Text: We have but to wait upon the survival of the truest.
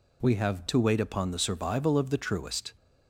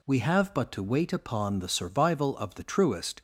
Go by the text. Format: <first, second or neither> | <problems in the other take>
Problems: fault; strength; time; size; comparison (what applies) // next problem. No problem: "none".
second | skips "but"; at 0.6 s